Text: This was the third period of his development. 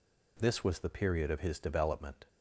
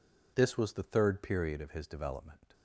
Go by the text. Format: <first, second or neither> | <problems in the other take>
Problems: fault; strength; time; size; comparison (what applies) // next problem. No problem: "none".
second | skips "third"; at 0.8 s